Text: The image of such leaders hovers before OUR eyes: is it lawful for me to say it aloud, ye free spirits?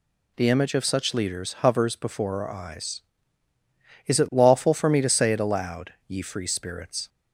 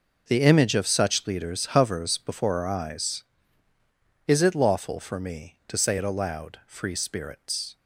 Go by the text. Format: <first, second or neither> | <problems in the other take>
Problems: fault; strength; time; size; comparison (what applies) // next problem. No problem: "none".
first | skips "ye"; at 6.6 s